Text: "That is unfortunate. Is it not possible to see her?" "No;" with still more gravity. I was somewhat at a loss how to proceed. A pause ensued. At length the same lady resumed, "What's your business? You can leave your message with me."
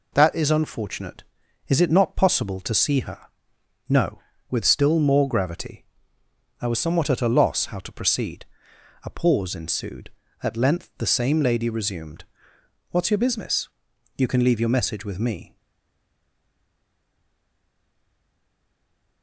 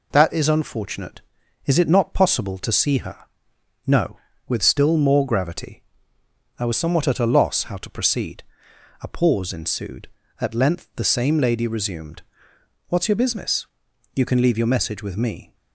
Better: second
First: stays silent after the last word; strong; from 15.5 s on; 3.7 s long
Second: none

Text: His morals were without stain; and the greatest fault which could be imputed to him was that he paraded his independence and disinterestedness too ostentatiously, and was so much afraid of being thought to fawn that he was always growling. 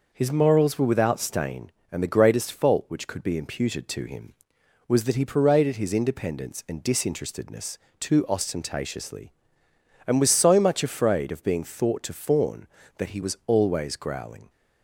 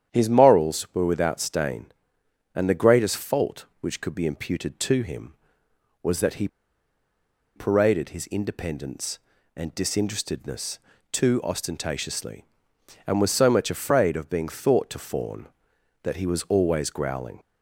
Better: first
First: pauses between "disinterestedness" and "too"; slight; at 7.7 s; 0.20 s long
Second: starts louder than the rest; strong; until 1.1 s; 9.5 dB // pauses between "he" and "paraded"; at 6.4 s; 1.0 s long // pauses between "disinterestedness" and "too"; slight; at 10.7 s; 0.36 s long

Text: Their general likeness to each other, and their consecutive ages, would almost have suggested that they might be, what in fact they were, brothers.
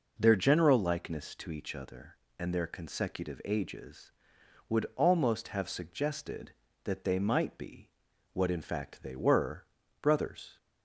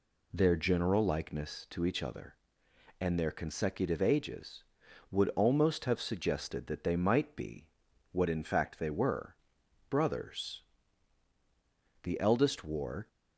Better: first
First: none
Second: goes on to say "The eldest wore"; noticeable; from 12.0 s on; 1.0 s long

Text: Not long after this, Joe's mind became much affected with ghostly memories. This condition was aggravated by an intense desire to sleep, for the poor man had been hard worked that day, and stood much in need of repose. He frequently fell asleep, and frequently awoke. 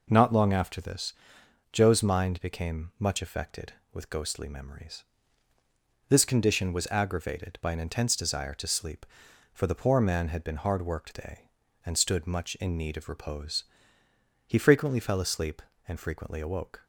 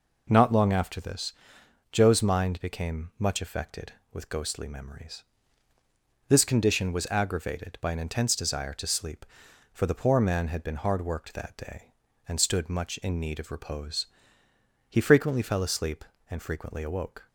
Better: second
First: skips "that"; at 11.1 s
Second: none

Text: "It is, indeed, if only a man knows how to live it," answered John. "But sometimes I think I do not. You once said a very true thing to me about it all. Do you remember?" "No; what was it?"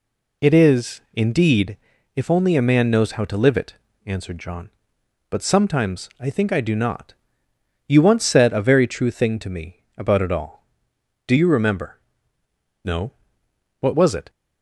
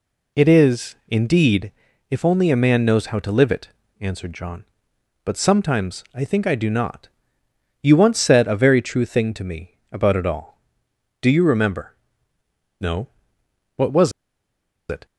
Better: first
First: none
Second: pauses between "was" and "it"; noticeable; at 14.1 s; 0.77 s long

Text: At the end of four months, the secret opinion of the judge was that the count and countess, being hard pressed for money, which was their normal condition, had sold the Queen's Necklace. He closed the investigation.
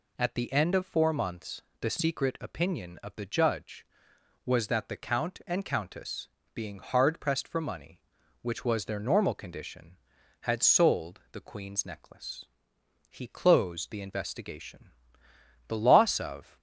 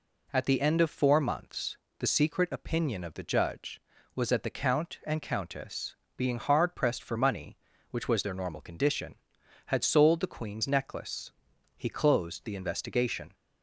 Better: second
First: goes on to say "The loss of"; noticeable; from 15.6 s on; 0.90 s long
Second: none

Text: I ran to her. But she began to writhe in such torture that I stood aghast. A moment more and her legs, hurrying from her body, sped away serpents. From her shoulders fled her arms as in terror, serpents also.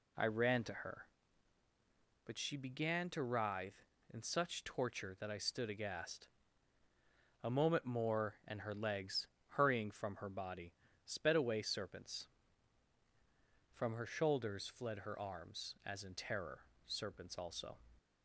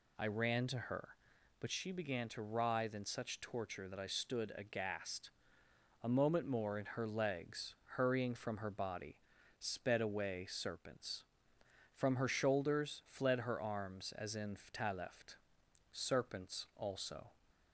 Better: first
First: none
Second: says "ftaleft" for "terror"; at 14.5 s

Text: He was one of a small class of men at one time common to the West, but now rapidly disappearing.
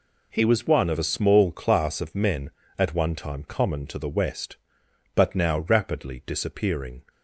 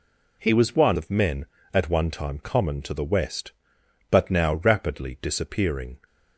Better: first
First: none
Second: skips "of a small class"; at 0.9 s

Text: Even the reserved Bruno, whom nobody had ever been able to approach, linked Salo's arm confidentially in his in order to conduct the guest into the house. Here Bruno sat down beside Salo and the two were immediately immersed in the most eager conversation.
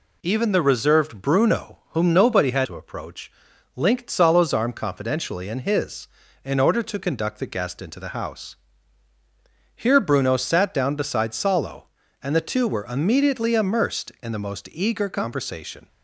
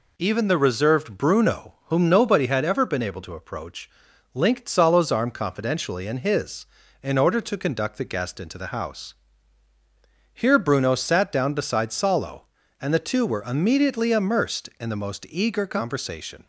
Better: second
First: skips "ever been able"; at 2.6 s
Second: none

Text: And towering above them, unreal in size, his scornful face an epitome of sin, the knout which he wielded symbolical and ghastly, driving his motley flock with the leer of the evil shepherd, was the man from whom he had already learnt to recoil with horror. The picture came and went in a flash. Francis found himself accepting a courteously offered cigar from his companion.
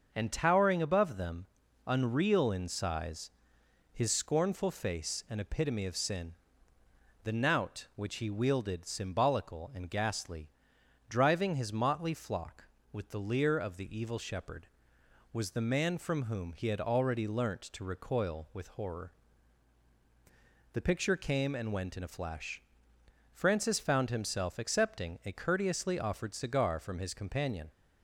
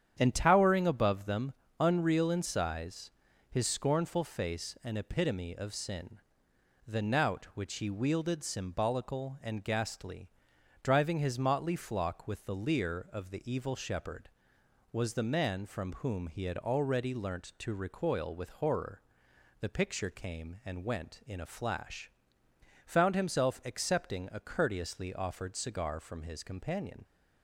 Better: first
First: starts louder than the rest; until 1.1 s; 6.5 dB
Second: starts louder than the rest; strong; until 1.2 s; 9 dB // skips "Francis"; at 22.4 s

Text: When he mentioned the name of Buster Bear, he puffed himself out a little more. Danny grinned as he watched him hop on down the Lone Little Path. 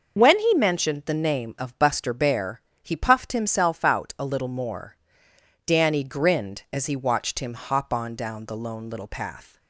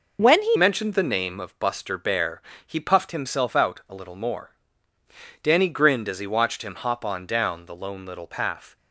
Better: first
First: none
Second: changes voice at "mentioned"; from 0.5 s on; 8.2 s long

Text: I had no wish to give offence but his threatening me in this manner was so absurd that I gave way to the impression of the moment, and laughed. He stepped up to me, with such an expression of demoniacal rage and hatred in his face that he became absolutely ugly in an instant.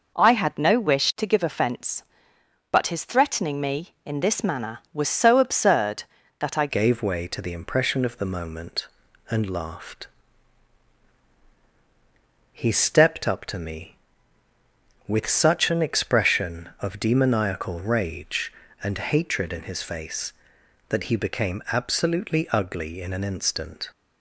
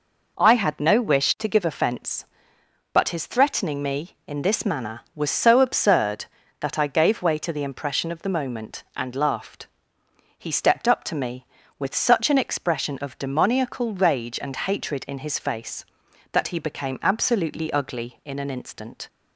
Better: second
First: changes voice at "gave"; from 6.6 s on; 17.2 s long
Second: none

